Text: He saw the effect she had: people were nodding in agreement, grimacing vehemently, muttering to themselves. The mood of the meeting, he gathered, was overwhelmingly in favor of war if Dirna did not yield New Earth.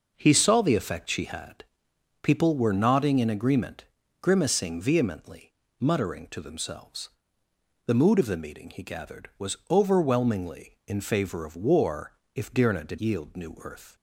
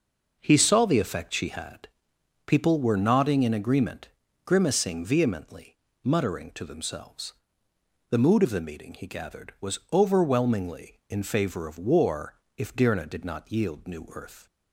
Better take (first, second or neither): second